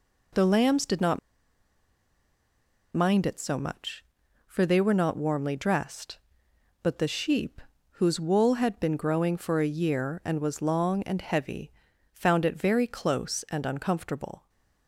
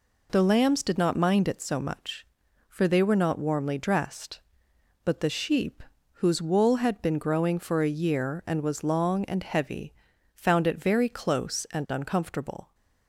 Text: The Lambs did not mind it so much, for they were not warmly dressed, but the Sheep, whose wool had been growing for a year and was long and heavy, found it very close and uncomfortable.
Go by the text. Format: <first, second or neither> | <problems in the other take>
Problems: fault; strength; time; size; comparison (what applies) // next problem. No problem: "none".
second | pauses between "not" and "mind"; strong; at 1.1 s; 1.7 s long